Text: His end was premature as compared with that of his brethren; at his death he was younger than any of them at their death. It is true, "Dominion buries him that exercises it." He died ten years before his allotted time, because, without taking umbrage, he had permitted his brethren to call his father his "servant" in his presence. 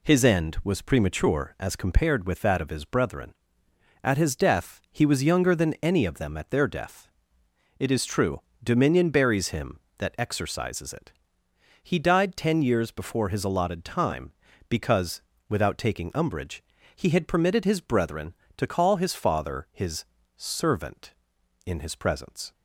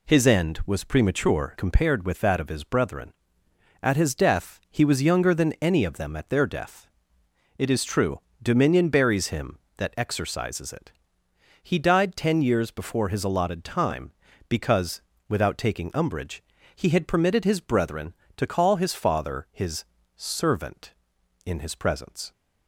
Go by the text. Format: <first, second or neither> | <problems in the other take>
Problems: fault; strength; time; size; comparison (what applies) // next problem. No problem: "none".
first | skips "as"; at 1.5 s // pauses between "his" and "servant"; slight; at 19.8 s; 0.32 s long; slight in the first